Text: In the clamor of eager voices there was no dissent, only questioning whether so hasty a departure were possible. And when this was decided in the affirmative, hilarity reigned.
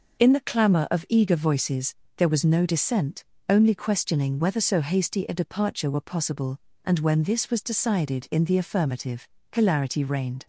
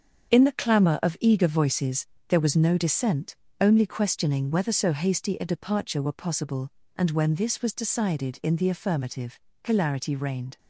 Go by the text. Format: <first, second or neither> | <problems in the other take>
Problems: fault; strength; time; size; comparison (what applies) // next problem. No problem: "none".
first | gets quieter; strong; throughout; 8 dB // pauses between "voices" and "there"; slight; at 2.0 s; 0.22 s long; slight in the first